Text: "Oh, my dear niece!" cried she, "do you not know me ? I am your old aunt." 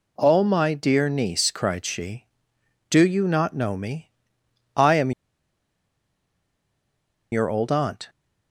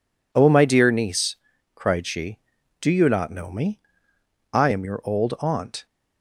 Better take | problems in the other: second | pauses between "am" and "your"; strong; at 5.1 s; 2.2 s long

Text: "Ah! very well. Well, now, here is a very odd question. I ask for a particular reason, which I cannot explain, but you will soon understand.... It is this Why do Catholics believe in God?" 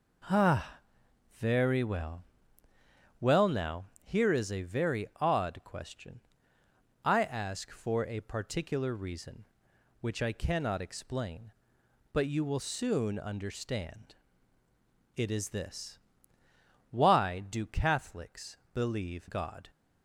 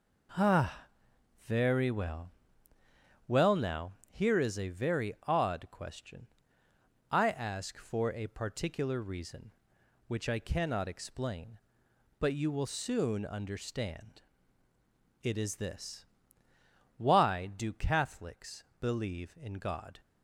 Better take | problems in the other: second | pauses between "this" and "Why"; noticeable; at 15.9 s; 0.90 s long; noticeable in the second // pauses between "Catholics" and "believe"; slight; at 18.5 s; 0.16 s long; slight in the second // skips "in"; at 19.2 s

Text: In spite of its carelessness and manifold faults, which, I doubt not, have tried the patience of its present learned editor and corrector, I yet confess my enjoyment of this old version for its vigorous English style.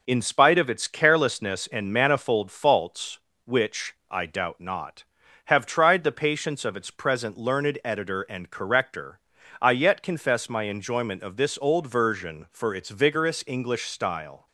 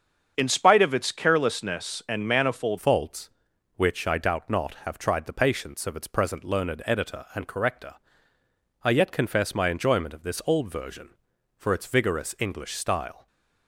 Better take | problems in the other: first | starts louder than the rest; until 1.3 s; 7 dB // changes voice at "faults"; from 2.7 s on; 10.5 s long

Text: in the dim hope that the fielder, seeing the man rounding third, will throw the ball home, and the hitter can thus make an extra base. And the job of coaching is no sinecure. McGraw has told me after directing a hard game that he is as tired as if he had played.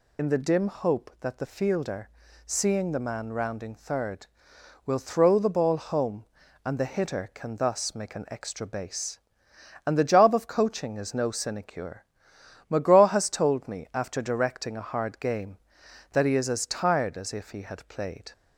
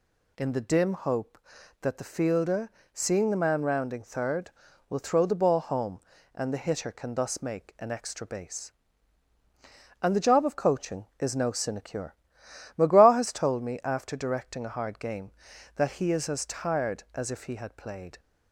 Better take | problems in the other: second | loses the start of "in"; at 0.1 s; 40 ms

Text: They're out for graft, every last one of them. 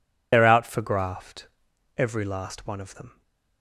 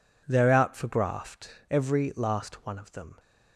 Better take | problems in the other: second | loses the start of "They're"; at 0.3 s; 50 ms

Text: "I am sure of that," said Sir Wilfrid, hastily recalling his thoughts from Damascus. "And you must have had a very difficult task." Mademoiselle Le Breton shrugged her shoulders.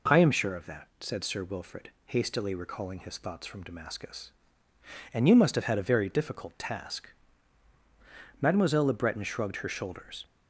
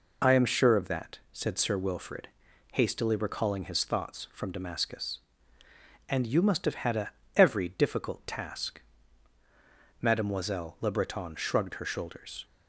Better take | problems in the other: first | says "every" for "very"; at 7.3 s

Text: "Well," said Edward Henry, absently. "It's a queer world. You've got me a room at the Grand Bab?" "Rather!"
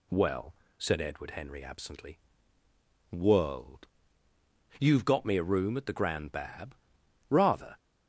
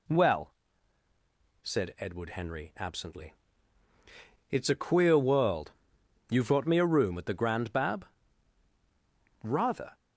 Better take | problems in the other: second | skips "It's a queer"; at 2.6 s

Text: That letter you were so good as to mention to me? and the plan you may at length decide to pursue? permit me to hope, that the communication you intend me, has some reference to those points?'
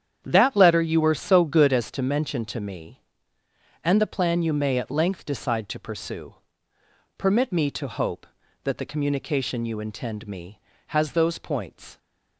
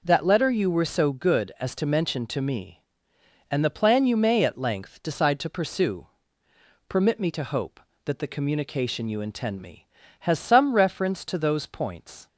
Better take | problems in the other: second | starts louder than the rest; strong; until 1.2 s; 9 dB // skips "some reference to"; at 11.1 s

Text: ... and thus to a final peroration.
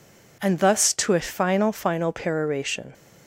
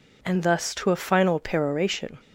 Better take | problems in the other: second | says "final" twice; at 1.7 s

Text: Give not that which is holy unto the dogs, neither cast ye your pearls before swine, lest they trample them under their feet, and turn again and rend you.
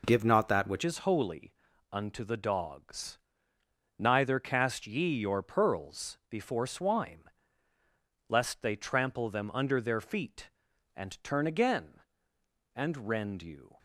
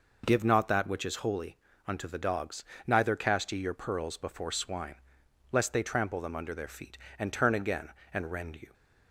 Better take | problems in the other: second | changes voice at "is"; from 0.8 s on; 12.9 s long // pauses between "holy" and "unto"; at 1.5 s; 0.38 s long; slight in the second

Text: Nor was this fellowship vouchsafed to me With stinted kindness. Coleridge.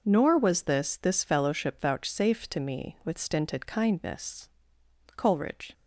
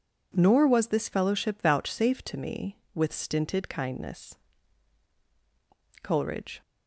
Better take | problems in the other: second | says "this" twice; at 1.0 s

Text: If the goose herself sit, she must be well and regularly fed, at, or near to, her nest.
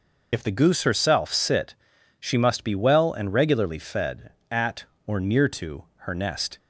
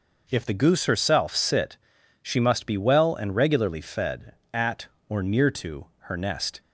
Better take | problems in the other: second | loses the start of "If"; at 0.3 s; 65 ms

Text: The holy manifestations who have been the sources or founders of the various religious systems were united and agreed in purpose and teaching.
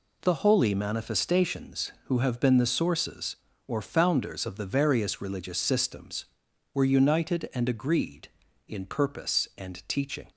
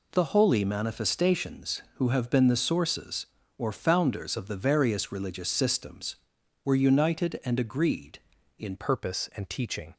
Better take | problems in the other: first | changes voice at "purpose"; from 8.7 s on; 1.2 s long

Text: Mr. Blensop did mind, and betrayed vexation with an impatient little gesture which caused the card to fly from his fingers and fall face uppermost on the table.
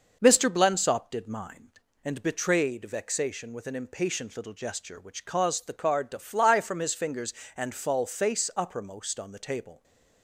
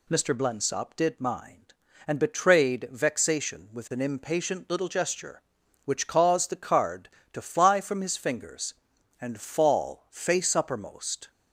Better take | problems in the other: first | stops before "on the table"; at 11.2 s

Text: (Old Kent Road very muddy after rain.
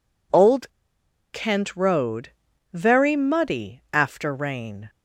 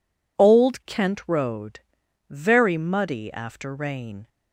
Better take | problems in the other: second | pauses between "Old" and "Kent"; noticeable; at 0.6 s; 0.62 s long // pauses between "Road" and "very"; at 2.3 s; 0.42 s long; noticeable in the second

